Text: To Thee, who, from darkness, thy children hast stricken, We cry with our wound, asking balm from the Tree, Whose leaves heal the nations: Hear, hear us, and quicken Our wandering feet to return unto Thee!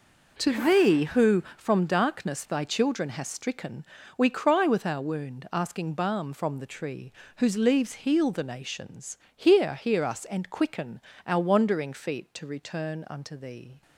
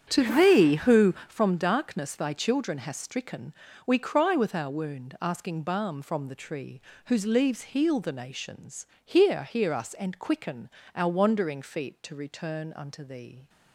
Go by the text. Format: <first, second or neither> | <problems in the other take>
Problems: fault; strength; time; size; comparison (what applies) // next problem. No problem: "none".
first | starts louder than the rest; strong; until 1.5 s; 8.5 dB // pauses between "quicken" and "Our"; slight; at 10.7 s; 0.24 s long; slight in the first